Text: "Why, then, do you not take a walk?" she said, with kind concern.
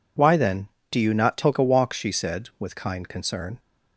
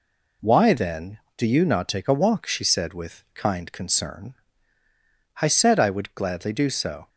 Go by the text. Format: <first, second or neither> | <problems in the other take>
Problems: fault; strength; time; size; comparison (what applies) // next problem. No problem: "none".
first | goes on to say "I said I would gladly do so"; strong; from 5.4 s on; 1.6 s long